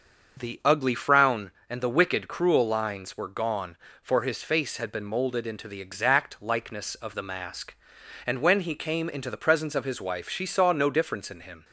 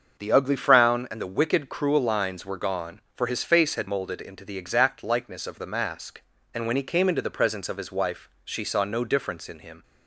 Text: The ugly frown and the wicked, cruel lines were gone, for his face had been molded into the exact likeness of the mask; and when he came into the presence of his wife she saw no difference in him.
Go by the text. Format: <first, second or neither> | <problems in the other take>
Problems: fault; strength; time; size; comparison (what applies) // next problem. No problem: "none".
first | starts louder than the rest; until 1.2 s; 6.5 dB; also in the first // skips "been"; at 3.8 s